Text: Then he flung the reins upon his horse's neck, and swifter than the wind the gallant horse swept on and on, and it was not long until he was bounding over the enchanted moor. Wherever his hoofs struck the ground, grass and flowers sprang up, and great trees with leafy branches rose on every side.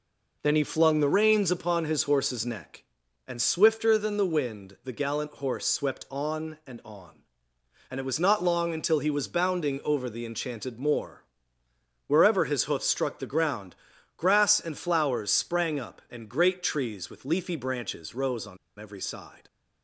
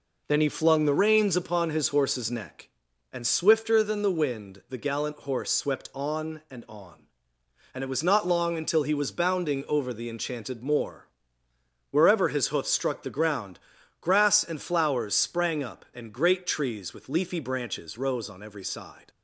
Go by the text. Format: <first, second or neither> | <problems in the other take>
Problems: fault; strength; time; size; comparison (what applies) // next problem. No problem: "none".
second | pauses between "on" and "every"; slight; at 18.5 s; 0.22 s long